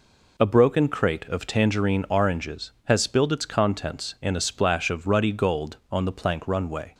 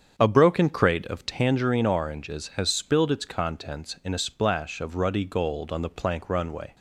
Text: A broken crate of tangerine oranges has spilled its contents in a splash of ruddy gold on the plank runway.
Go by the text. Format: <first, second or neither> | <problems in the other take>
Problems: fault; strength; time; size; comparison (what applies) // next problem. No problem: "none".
first | starts louder than the rest; strong; until 1.5 s; 8 dB